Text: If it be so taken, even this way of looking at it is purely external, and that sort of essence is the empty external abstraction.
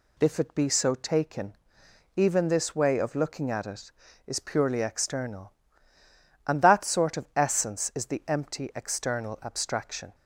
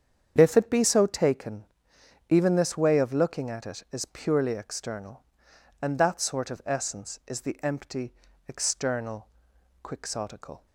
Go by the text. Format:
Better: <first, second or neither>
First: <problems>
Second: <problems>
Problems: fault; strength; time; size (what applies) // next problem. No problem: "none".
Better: first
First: none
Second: starts louder than the rest; strong; until 1.3 s; 8.5 dB // pauses between "empty" and "external"; slight; at 8.1 s; 0.34 s long // says "quixotical" for "abstraction"; at 9.8 s